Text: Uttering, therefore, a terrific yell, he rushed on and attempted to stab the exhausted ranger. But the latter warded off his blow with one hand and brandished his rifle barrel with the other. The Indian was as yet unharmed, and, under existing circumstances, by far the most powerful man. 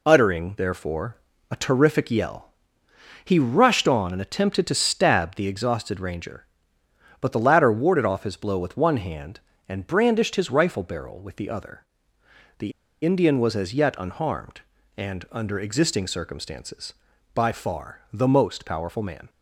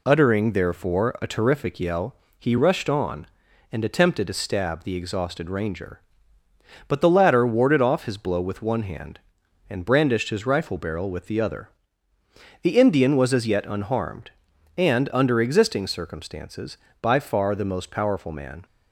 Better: second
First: pauses between "The" and "Indian"; slight; at 12.7 s; 0.33 s long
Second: none

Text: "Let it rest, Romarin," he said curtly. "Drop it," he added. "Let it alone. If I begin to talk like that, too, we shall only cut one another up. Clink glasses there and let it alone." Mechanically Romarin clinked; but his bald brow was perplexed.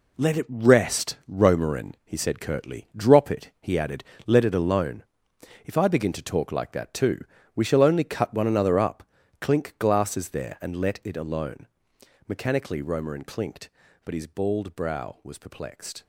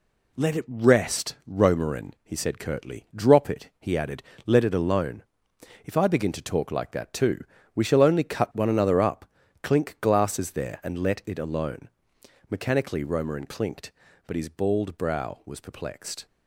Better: second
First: gets quieter; strong; throughout; 8 dB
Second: none

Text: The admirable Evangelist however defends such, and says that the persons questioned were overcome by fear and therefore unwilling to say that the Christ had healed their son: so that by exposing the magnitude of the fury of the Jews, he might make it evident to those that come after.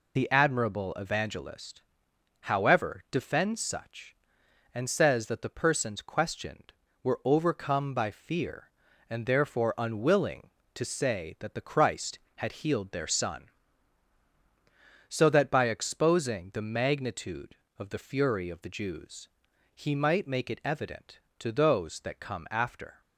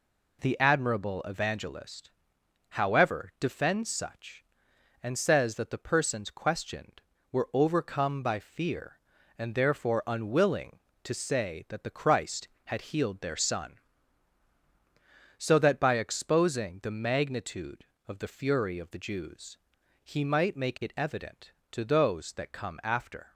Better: second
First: loses the start of "The"; at 0.1 s; 40 ms // pauses between "Evangelist" and "however"; noticeable; at 1.8 s; 0.64 s long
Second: pauses between "Evangelist" and "however"; noticeable; at 2.0 s; 0.64 s long

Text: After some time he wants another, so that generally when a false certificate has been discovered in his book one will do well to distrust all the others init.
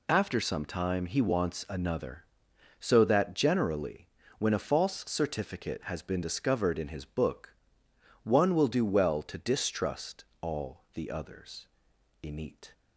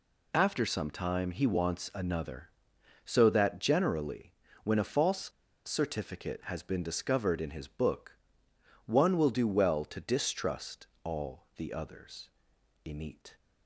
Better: first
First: pauses between "generally" and "when"; slight; at 4.0 s; 0.28 s long // pauses between "book" and "one"; noticeable; at 7.5 s; 0.70 s long // pauses between "distrust" and "all"; slight; at 10.2 s; 0.16 s long // pauses between "others" and "init"; noticeable; at 11.6 s; 0.56 s long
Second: pauses between "generally" and "when"; slight; at 4.3 s; 0.28 s long // pauses between "false" and "certificate"; slight; at 5.3 s; 0.35 s long // pauses between "book" and "one"; noticeable; at 8.1 s; 0.70 s long // pauses between "distrust" and "all"; slight; at 10.8 s; 0.16 s long // pauses between "others" and "init"; noticeable; at 12.2 s; 0.56 s long

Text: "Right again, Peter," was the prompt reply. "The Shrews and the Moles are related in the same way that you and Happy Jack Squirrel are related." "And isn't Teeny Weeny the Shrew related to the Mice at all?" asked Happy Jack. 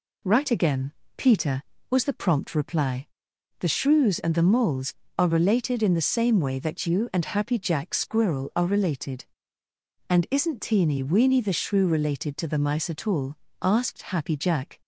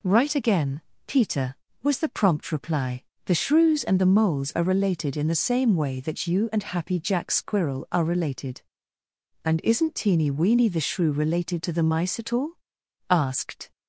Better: first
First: none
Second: stops before "Happy Jack"; at 13.7 s

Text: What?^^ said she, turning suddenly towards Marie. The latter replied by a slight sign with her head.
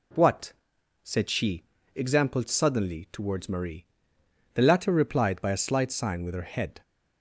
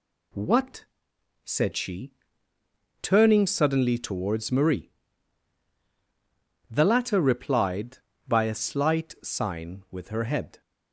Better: second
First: says "exampled" for "turning"; at 1.9 s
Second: none

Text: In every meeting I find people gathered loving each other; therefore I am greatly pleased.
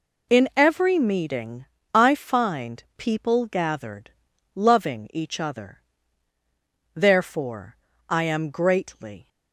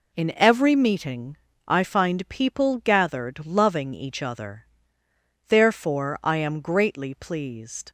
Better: second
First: pauses between "meeting" and "I"; slight; at 1.6 s; 0.26 s long // pauses between "gathered" and "loving"; at 4.1 s; 0.44 s long // pauses between "therefore" and "I"; slight; at 7.7 s; 0.32 s long // stops before "pleased"; at 9.2 s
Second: pauses between "meeting" and "I"; slight; at 1.3 s; 0.28 s long

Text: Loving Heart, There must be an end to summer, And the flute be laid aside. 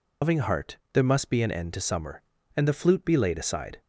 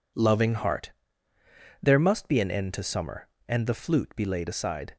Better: second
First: loses the start of "Loving"; at 0.2 s; 135 ms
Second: none

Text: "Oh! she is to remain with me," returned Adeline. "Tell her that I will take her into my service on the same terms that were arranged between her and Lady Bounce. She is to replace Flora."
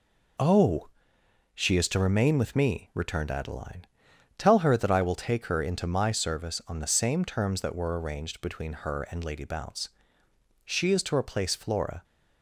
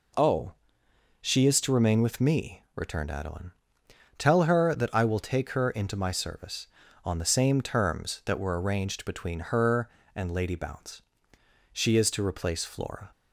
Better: neither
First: none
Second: none

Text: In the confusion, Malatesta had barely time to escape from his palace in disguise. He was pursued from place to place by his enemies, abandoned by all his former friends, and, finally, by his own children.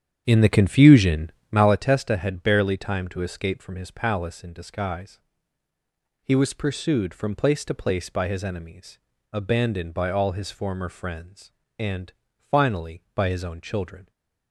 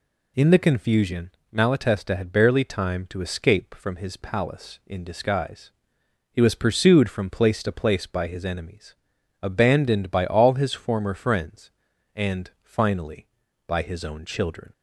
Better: second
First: starts louder than the rest; strong; until 1.8 s; 8.5 dB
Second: none

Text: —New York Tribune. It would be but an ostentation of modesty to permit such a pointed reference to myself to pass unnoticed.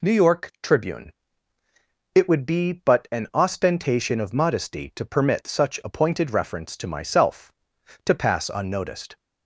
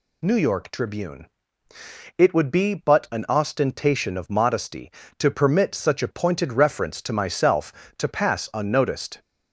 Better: neither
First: none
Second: none

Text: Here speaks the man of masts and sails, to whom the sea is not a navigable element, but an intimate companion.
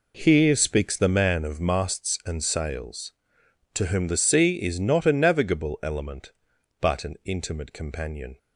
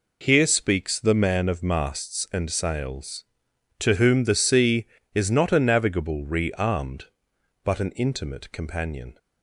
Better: first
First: none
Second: says "rearmed" for "element"; at 6.2 s

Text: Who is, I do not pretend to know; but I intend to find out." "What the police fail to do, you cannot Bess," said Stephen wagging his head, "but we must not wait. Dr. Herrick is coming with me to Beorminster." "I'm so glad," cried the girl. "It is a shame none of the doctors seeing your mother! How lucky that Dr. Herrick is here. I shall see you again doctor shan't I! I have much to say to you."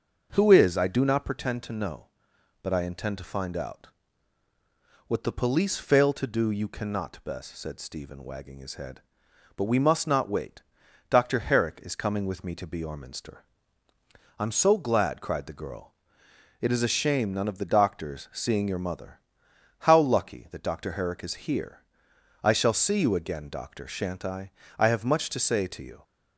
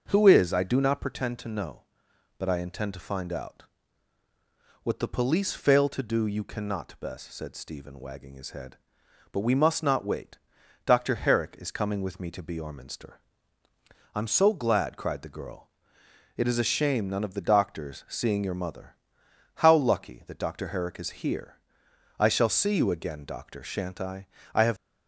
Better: first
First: none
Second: stops before "much to say to you"; at 24.7 s

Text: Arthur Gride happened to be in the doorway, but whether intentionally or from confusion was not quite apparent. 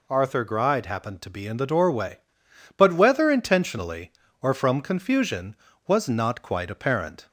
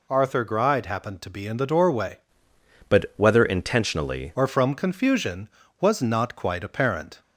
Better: first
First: none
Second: changes voice from "but" to "intentionally"; from 2.8 to 4.3 s; 1.5 s long

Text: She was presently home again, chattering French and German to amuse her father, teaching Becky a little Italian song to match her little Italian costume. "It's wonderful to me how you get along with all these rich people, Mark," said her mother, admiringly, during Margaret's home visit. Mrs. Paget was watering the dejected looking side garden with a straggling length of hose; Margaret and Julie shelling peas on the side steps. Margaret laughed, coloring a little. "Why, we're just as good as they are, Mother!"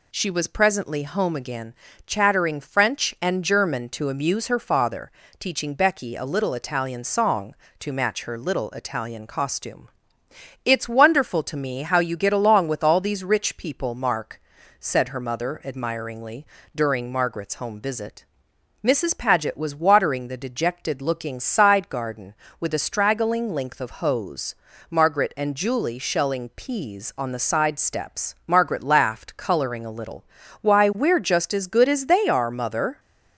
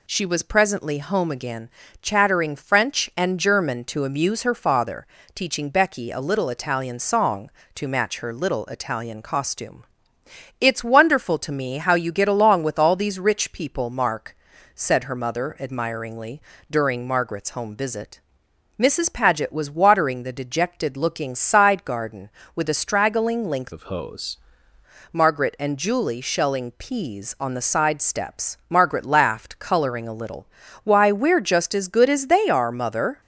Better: first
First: none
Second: changes voice from "of" to "hose"; from 23.7 to 24.3 s; 0.6 s long

